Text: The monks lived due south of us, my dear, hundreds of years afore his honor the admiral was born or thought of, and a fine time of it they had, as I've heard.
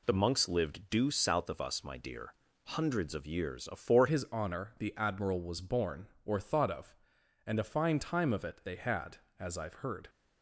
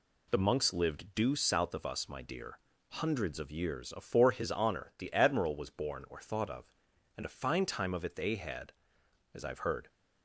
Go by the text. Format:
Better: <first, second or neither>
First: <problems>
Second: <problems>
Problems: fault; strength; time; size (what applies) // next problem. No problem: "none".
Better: second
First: changes voice at "his"; from 4.0 s on; 6.0 s long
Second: none